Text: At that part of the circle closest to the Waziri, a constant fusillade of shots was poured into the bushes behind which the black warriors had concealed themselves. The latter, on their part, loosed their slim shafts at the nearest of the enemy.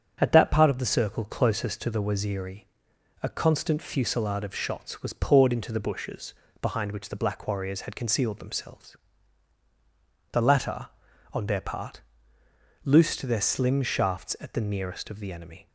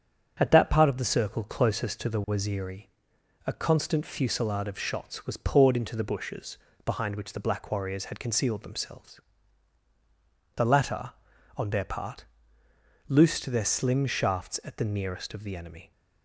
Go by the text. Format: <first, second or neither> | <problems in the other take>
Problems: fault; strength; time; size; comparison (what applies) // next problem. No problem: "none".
neither | starts louder than the rest; strong; the same in both // pauses between "bushes" and "behind"; slight; the same in both